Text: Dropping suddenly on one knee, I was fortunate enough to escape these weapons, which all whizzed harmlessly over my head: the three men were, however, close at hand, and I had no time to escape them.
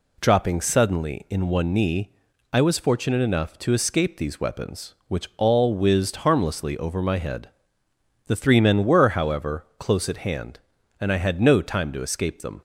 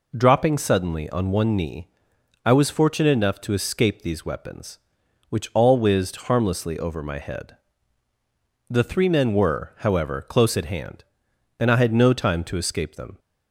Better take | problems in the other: second | says "in" for "on"; at 1.2 s

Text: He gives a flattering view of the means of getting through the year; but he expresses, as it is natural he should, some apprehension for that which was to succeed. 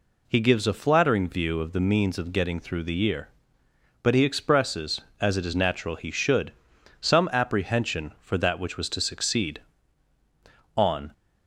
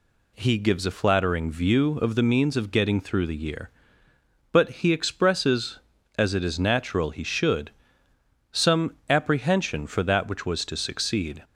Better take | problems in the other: second | goes on to say "On"; slight; from 10.7 s on; 0.36 s long

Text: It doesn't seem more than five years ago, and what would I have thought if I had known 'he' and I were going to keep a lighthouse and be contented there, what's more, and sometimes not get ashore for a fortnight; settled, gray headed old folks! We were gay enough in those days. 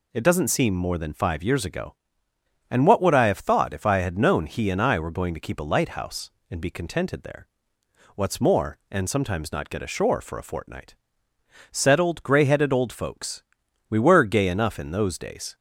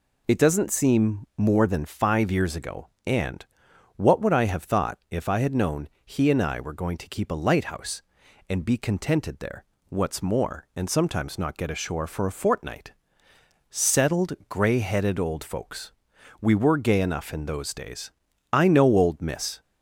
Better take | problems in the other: first | pauses between "and" and "what"; noticeable; at 3.4 s; 0.52 s long // pauses between "known" and "he"; slight; at 5.8 s; 0.16 s long // goes on to say "I know old Miss"; noticeable; from 18.5 s on; 1.1 s long

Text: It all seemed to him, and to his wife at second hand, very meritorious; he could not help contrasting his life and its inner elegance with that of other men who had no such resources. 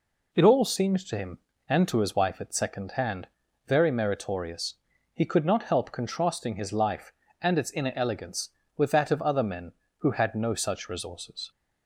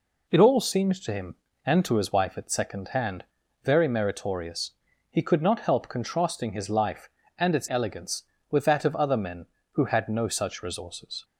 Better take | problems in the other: first | skips "inner"; at 7.6 s

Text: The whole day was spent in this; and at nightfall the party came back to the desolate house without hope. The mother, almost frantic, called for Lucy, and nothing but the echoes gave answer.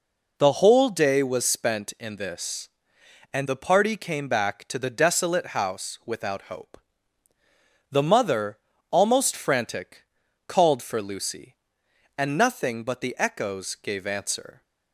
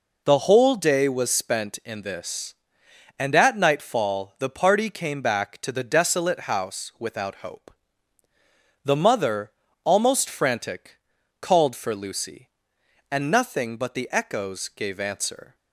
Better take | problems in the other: second | skips "at nightfall"; at 3.4 s

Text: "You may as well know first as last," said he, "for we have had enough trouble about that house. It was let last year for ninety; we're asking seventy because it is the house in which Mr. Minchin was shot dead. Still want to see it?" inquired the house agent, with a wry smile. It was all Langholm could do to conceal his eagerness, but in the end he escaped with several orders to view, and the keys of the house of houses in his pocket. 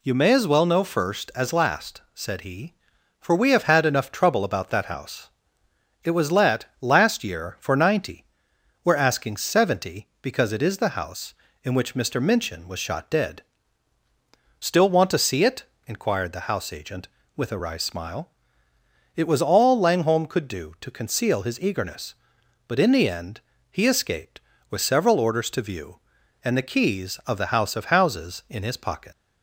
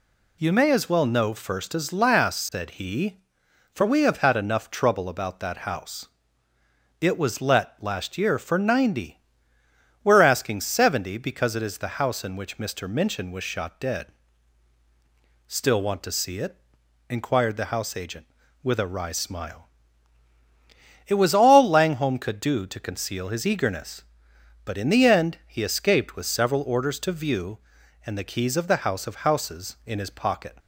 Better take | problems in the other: second | pauses between "let" and "last"; slight; at 6.6 s; 0.16 s long // pauses between "end" and "he"; slight; at 23.4 s; 0.28 s long // leaves "pocket" unfinished; at 29.1 s; 70 ms

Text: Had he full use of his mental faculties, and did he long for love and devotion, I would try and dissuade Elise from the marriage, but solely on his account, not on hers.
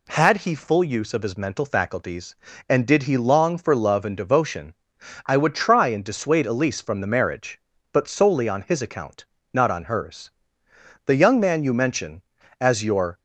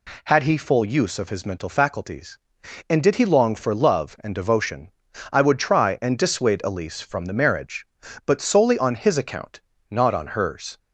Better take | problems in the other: second | goes on to say "The young man you mention as your"; strong; from 11.0 s on; 2.1 s long

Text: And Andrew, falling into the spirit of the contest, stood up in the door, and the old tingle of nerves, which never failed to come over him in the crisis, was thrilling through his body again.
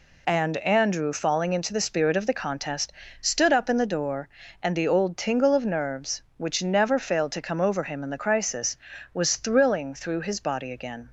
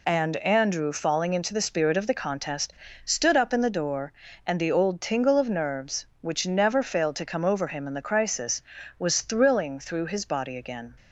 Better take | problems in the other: neither | none

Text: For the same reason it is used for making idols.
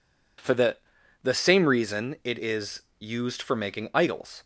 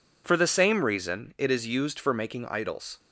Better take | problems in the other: second | says "the" twice; at 1.2 s // pauses between "is" and "used"; slight; at 2.8 s; 0.16 s long

